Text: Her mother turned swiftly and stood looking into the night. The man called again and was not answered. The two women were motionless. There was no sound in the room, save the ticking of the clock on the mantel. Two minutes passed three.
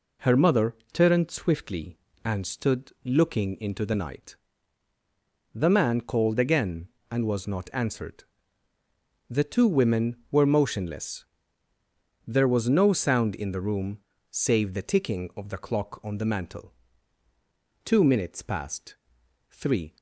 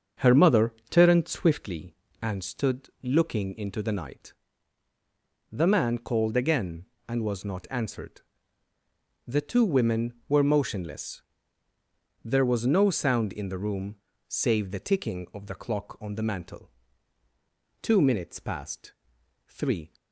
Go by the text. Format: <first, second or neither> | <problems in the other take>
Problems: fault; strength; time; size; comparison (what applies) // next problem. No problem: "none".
first | starts louder than the rest; until 1.8 s; 7 dB // pauses between "mother" and "turned"; slight; at 0.7 s; 0.17 s long; slight in the first // pauses between "passed" and "three"; noticeable; at 18.9 s; 0.56 s long; noticeable in the first